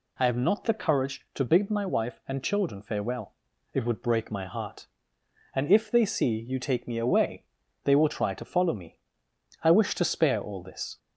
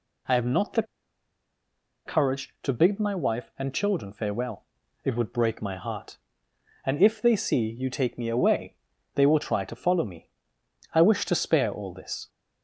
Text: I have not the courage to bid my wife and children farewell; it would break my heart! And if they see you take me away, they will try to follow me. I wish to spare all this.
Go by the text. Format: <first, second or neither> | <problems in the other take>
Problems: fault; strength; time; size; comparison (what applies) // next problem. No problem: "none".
first | pauses between "the" and "courage"; at 0.8 s; 1.2 s long